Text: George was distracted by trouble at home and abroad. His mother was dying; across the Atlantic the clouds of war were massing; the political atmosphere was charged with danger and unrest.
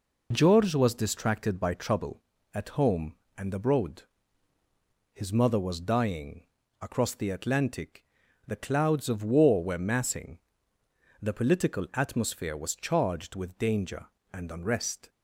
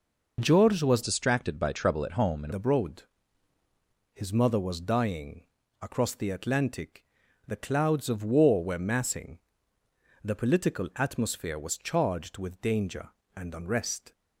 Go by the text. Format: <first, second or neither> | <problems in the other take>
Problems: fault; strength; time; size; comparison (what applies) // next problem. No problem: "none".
first | changes voice from "distracted" to "and"; from 1.0 to 2.5 s; 1.5 s long // pauses between "Atlantic" and "the"; at 7.0 s; 0.42 s long; also in the first